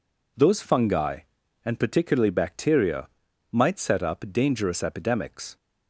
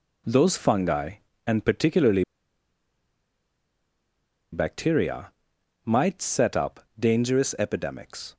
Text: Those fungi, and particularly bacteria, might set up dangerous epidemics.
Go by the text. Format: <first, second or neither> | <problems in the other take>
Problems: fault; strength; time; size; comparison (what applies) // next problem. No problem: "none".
first | pauses between "particularly" and "bacteria"; strong; at 2.2 s; 2.2 s long // pauses between "up" and "dangerous"; slight; at 6.8 s; 0.18 s long